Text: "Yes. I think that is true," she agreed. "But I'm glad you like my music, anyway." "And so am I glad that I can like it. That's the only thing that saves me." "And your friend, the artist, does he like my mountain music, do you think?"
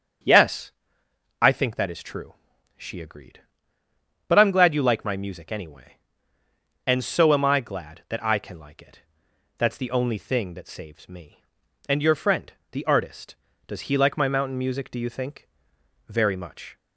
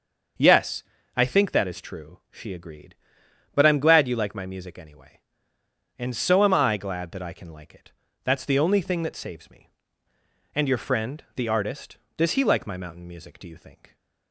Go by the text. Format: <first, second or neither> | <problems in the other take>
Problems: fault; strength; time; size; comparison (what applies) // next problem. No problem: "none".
second | starts louder than the rest; strong; until 1.9 s; 7.5 dB; also in the second // goes on to say "Very much"; noticeable; from 16.0 s on; 0.70 s long